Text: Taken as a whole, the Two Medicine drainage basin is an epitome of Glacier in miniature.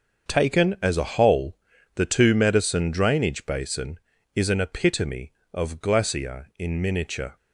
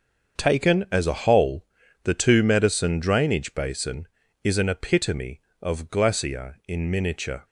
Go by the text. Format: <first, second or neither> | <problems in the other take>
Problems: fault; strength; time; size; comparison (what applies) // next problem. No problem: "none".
neither | starts louder than the rest; the same in both